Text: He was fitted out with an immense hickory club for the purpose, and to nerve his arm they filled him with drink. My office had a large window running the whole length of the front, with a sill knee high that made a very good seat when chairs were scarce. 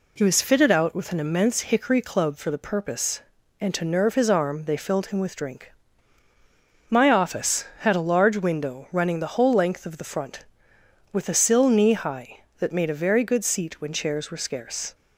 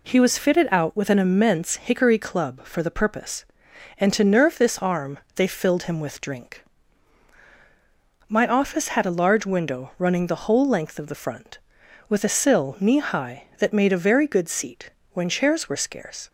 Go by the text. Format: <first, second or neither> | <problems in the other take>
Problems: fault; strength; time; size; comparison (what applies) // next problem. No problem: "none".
first | says "this" for "his"; at 4.5 s // pauses between "arm" and "they"; slight; at 5.1 s; 0.16 s long // pauses between "seat" and "when"; slight; at 14.9 s; 0.22 s long